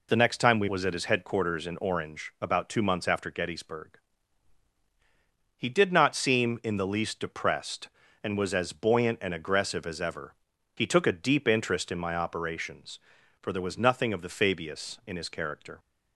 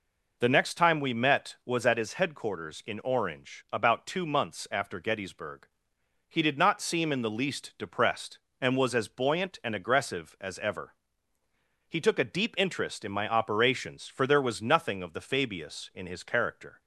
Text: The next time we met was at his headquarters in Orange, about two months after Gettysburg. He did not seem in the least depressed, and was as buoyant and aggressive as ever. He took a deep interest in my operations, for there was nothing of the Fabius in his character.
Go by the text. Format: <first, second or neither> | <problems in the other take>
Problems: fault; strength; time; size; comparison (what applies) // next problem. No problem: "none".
second | skips "met"; at 0.6 s